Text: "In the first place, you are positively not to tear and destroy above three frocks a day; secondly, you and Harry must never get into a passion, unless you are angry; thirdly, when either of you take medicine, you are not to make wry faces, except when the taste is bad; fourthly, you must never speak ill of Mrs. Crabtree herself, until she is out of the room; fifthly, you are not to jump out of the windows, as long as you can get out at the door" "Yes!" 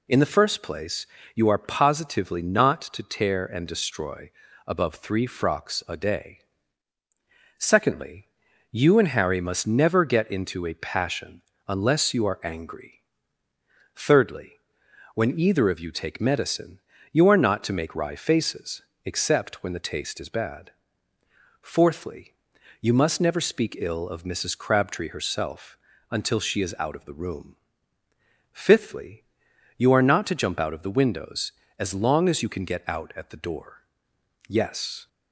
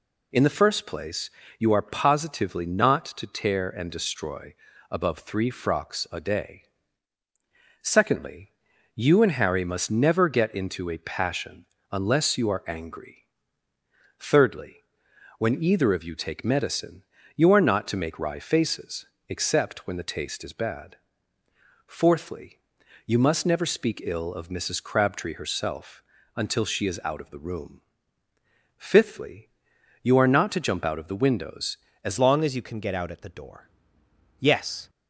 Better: first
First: pauses between "destroy" and "above"; slight; at 4.3 s; 0.36 s long // pauses between "door" and "Yes"; noticeable; at 33.8 s; 0.66 s long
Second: pauses between "destroy" and "above"; slight; at 4.5 s; 0.36 s long // changes voice at "long"; from 32.1 s on; 2.7 s long // pauses between "door" and "Yes"; noticeable; at 33.6 s; 0.70 s long

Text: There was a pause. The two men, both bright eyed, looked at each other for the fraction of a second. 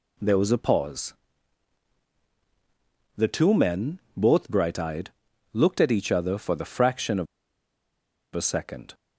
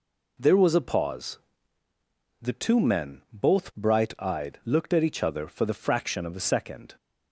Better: second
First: pauses between "of" and "a"; at 7.2 s; 1.0 s long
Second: none

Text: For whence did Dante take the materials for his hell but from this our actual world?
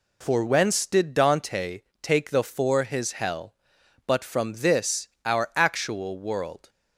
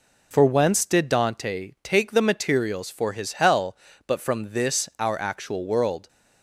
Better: second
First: pauses between "Dante" and "take"; slight; at 1.8 s; 0.22 s long // skips "materials"; at 2.4 s // pauses between "this" and "our"; slight; at 5.0 s; 0.18 s long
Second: none

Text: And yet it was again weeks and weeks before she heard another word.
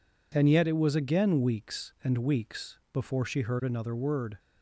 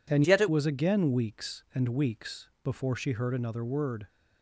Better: first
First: none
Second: changes voice from "yet" to "it"; from 0.2 to 0.4 s; 0.2 s long

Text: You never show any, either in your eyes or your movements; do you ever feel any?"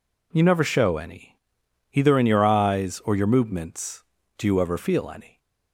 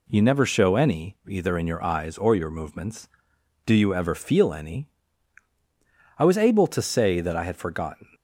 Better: first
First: none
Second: goes on to say "I was able to say that I had forgotten"; strong; from 6.1 s on; 1.9 s long

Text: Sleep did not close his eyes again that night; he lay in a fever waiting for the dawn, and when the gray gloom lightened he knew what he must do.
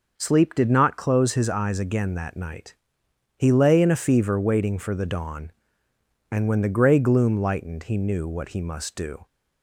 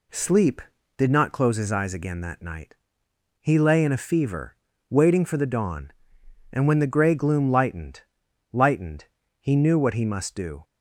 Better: first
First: none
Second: pauses between "fever" and "waiting"; slight; at 4.5 s; 0.34 s long // says "lightened" twice; at 8.5 s

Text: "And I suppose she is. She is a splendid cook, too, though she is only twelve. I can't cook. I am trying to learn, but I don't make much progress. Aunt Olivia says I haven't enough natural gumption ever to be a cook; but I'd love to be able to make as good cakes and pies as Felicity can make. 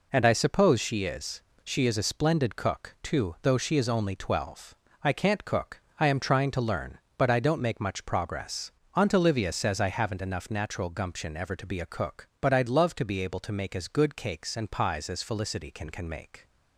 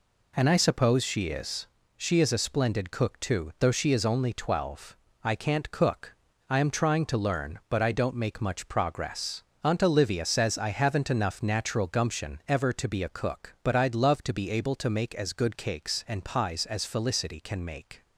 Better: second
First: says "can" twice; at 15.9 s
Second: none

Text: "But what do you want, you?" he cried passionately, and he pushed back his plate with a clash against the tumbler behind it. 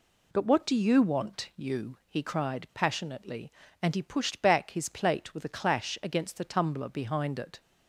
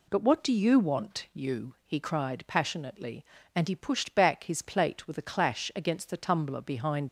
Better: first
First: none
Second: stops before "it"; at 7.0 s

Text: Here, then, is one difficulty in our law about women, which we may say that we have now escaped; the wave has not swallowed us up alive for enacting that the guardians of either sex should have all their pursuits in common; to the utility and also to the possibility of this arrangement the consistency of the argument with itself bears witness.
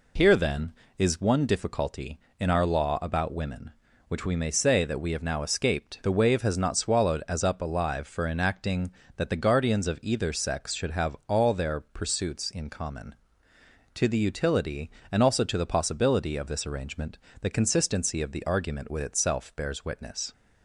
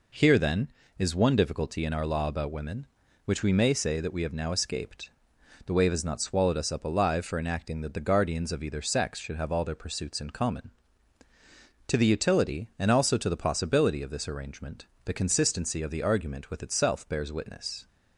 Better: second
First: says "as" for "us"; at 7.2 s // pauses between "arrangement" and "the"; slight; at 17.1 s; 0.24 s long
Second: pauses between "arrangement" and "the"; slight; at 14.8 s; 0.20 s long

